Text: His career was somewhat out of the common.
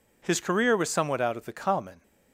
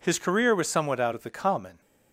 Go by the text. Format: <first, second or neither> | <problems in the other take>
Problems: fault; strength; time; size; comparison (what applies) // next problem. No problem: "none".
neither | none